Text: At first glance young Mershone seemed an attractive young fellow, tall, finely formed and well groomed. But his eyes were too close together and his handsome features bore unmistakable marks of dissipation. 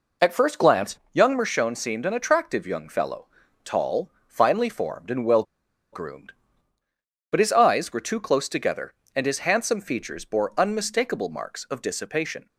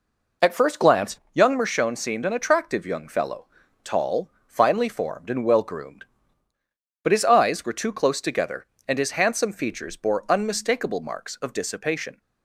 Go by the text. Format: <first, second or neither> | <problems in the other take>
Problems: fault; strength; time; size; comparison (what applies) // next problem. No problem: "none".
second | pauses between "well" and "groomed"; noticeable; at 5.4 s; 0.49 s long